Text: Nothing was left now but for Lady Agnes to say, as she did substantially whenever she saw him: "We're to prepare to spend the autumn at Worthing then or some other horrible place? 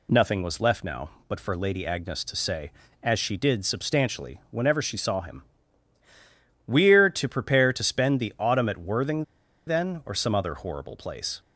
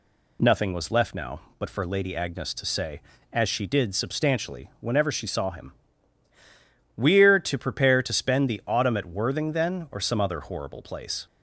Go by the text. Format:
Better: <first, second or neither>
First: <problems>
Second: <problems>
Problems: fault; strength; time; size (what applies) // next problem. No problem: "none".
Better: second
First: pauses between "Worthing" and "then"; at 9.2 s; 0.44 s long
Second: none